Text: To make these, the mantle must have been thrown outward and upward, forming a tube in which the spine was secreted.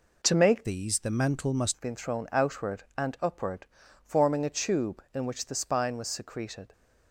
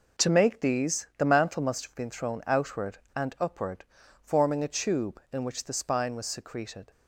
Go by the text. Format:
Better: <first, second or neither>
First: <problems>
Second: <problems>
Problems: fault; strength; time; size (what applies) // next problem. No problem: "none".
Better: second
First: changes voice from "these" to "must"; from 0.6 to 1.7 s; 1.1 s long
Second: none